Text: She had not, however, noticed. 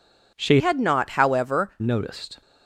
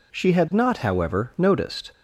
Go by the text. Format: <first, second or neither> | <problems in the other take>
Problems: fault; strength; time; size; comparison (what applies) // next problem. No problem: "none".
second | changes voice from "had" to "however"; from 0.5 to 1.6 s; 1.1 s long